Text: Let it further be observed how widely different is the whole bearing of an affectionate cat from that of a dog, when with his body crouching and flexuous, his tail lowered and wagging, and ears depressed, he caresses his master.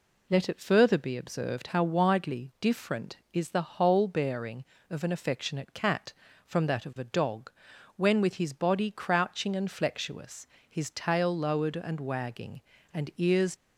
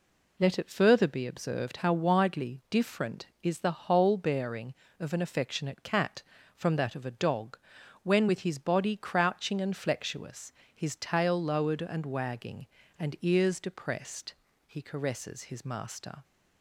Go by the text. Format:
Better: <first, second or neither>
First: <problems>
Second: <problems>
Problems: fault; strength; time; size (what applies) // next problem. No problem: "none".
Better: second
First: stops before "depressed he caresses his master"; at 13.5 s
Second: none